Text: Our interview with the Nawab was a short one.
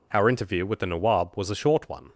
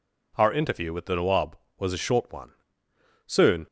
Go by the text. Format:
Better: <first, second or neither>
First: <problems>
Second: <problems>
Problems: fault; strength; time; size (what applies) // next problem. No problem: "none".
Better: first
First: none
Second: goes on to say "Soon"; slight; from 3.2 s on; 0.40 s long